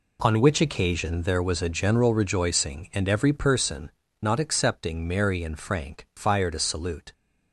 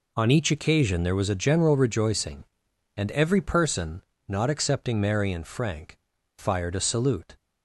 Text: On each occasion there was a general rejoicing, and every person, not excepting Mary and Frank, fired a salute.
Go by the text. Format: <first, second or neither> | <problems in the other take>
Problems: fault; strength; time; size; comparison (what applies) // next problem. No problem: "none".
second | says "which" for "each"; at 0.3 s